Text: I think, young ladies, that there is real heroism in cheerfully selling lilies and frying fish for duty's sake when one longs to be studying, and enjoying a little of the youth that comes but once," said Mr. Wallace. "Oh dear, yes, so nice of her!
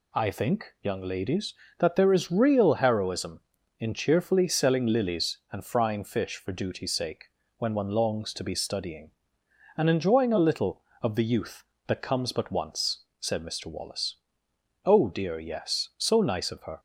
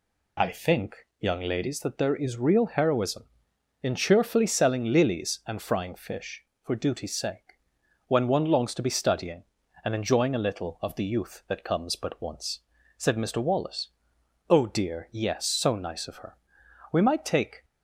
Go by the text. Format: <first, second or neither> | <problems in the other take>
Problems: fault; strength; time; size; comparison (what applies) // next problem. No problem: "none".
first | pauses between "sake" and "when"; noticeable; at 7.5 s; 0.48 s long; slight in the first // goes on to say "We might take"; noticeable; from 16.9 s on; 0.72 s long